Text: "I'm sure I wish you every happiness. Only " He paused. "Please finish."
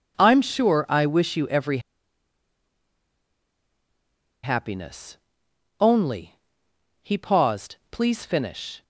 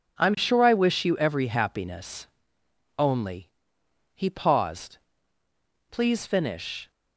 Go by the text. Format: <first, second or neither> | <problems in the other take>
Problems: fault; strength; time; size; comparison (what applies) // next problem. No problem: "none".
second | pauses between "every" and "happiness"; strong; at 1.7 s; 2.6 s long